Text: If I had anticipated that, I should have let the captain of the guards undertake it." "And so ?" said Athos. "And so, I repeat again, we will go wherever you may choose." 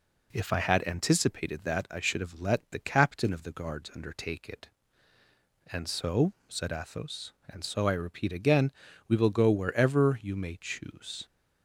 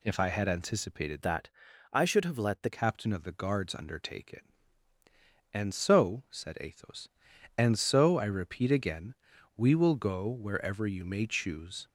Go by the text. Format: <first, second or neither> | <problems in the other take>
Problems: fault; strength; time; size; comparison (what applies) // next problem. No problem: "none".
first | changes voice from "that" to "the"; from 1.2 to 2.7 s; 1.5 s long